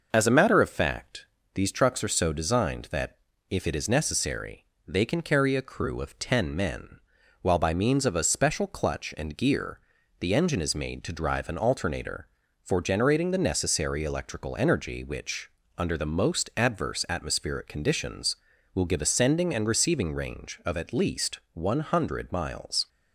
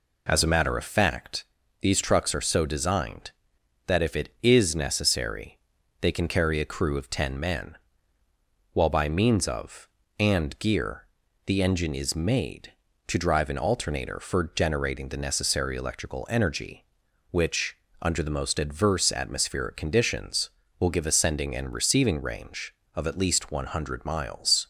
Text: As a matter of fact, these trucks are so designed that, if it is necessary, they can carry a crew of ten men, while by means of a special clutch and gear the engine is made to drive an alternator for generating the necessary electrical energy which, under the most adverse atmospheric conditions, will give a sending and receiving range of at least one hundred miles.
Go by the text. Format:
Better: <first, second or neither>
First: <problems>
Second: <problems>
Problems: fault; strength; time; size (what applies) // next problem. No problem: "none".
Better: first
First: pauses between "gear" and "the"; at 9.8 s; 0.40 s long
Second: skips "a special clutch"; at 10.0 s // pauses between "gear" and "the"; at 11.0 s; 0.40 s long